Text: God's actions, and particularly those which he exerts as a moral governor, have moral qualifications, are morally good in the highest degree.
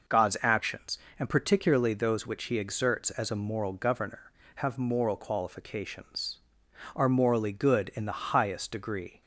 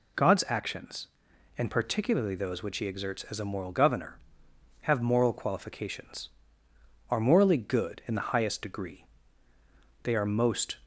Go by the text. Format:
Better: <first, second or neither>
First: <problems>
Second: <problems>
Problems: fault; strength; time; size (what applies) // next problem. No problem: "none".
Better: first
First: none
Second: goes on to say "They are most"; noticeable; from 10.0 s on; 0.74 s long